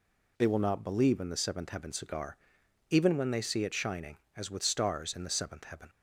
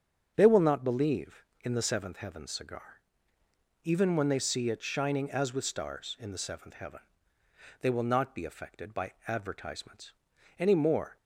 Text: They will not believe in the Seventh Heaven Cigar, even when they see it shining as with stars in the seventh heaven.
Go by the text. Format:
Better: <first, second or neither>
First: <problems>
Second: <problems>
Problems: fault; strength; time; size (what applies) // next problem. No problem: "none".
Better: first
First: none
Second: starts louder than the rest; strong; until 1.3 s; 7 dB // goes on to say "They will not be affected by advertisements any more"; strong; from 7.8 s on; 3.3 s long